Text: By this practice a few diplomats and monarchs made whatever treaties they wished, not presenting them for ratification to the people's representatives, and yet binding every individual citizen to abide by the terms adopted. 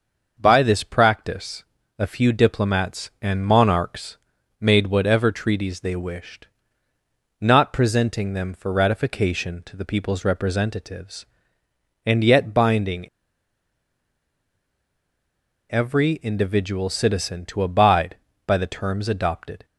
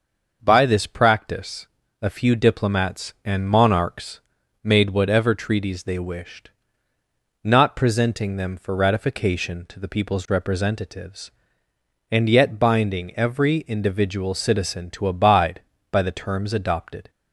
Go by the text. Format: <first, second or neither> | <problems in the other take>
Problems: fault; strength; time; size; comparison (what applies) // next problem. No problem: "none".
second | starts louder than the rest; until 1.3 s; 6.5 dB; also in the second // pauses between "practice" and "a"; slight; at 1.6 s; 0.34 s long; slight in the second // pauses between "monarchs" and "made"; at 4.1 s; 0.42 s long; also in the second // pauses between "binding" and "every"; strong; at 13.0 s; 2.6 s long